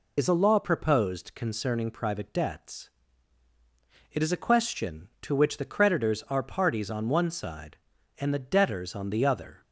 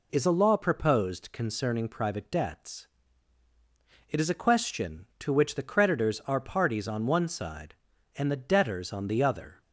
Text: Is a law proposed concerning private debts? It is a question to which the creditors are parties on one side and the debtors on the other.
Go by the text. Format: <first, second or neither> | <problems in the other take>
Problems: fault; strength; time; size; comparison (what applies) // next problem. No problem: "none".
second | loses the start of "Is"; at 0.1 s; 45 ms